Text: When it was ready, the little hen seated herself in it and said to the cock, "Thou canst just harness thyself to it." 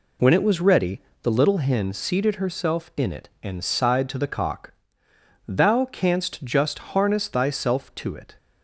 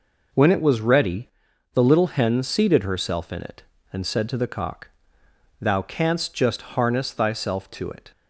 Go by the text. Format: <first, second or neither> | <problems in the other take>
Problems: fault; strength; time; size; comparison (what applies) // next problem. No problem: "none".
second | says "sighed" for "said"; at 3.6 s